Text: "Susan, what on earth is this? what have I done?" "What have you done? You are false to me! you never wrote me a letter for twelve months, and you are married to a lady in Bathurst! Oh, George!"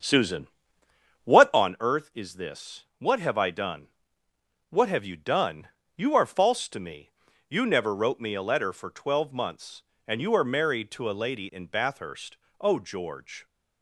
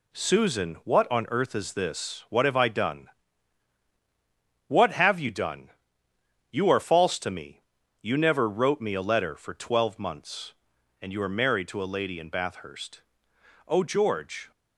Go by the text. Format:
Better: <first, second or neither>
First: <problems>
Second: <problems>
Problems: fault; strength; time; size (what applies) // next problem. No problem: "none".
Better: second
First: starts louder than the rest; strong; until 1.7 s; 7.5 dB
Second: none